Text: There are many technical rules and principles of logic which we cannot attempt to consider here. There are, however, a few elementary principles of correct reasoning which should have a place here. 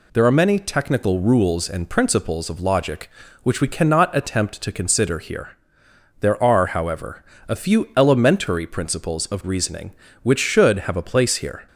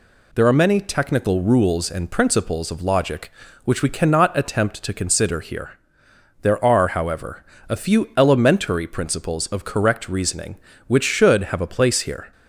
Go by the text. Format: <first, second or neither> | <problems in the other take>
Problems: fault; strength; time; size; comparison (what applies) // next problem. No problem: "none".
second | skips "correct"; at 9.4 s